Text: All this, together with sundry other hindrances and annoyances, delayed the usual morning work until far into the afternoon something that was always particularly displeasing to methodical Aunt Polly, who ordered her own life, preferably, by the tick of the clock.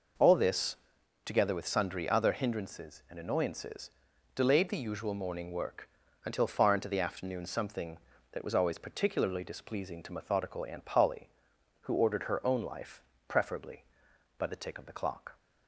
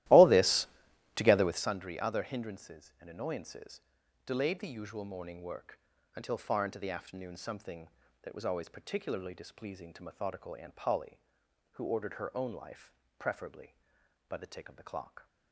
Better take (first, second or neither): first